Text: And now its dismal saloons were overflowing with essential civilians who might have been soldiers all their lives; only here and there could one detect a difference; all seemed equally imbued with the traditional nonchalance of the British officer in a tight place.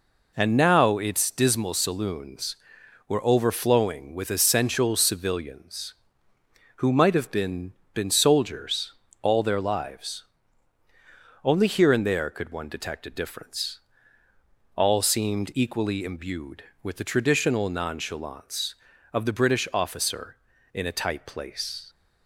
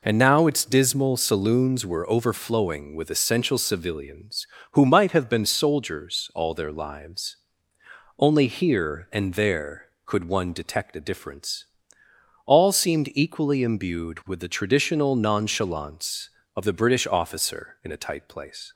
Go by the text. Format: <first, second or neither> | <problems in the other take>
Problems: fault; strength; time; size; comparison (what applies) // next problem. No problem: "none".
second | says "been" twice; at 7.9 s // pauses between "soldiers" and "all"; slight; at 8.9 s; 0.28 s long